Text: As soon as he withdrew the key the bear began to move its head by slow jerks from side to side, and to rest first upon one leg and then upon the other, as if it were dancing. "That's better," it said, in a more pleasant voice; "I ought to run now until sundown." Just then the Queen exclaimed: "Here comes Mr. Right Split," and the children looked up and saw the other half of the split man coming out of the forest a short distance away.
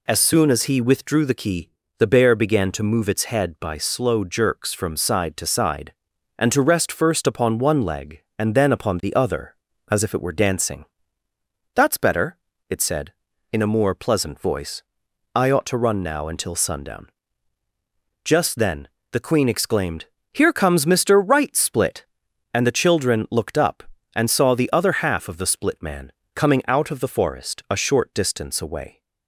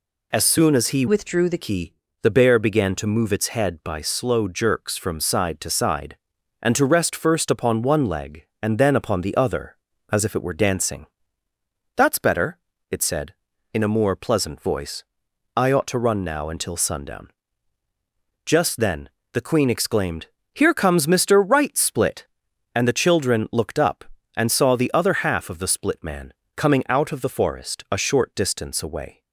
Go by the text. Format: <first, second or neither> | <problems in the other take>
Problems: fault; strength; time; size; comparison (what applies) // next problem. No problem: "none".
first | changes voice from "withdrew" to "the"; from 1.0 to 1.5 s; 0.5 s long // pauses between "key" and "the"; slight; at 1.9 s; 0.30 s long; slight in the first // pauses between "then" and "the"; slight; at 19.0 s; 0.24 s long; slight in the first // pauses between "man" and "coming"; slight; at 26.3 s; 0.22 s long; slight in the first